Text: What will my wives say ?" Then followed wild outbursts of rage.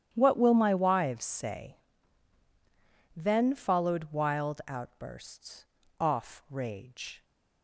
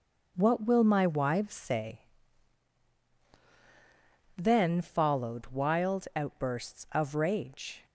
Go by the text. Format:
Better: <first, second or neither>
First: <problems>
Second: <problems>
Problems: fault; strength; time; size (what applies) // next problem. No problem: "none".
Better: second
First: starts louder than the rest; strong; until 1.1 s; 9 dB // says "off" for "of"; at 6.0 s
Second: none